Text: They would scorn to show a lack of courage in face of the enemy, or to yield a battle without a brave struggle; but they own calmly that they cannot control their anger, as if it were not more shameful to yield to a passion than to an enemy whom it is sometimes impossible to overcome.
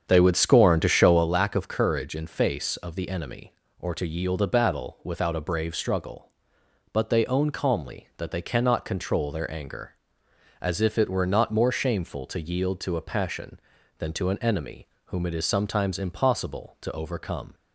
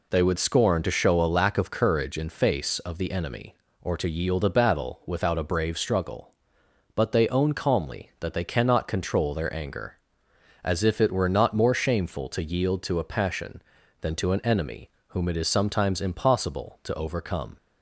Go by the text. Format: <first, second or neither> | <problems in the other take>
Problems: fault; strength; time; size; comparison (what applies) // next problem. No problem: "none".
second | starts louder than the rest; strong; until 1.3 s; 8 dB // pauses between "enemy" and "whom"; slight; at 14.8 s; 0.20 s long; slight in the second